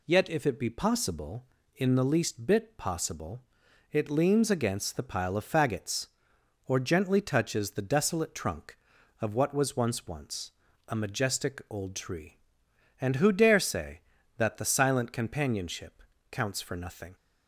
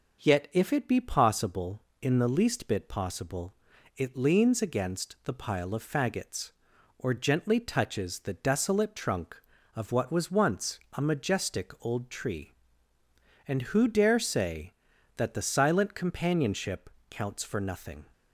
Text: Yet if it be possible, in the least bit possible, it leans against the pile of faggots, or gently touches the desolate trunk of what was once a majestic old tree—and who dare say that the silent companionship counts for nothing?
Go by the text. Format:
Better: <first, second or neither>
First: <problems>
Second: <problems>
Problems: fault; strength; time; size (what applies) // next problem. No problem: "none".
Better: second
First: says "once" twice; at 10.0 s // pauses between "companionship" and "counts"; slight; at 16.0 s; 0.28 s long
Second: pauses between "companionship" and "counts"; slight; at 16.9 s; 0.20 s long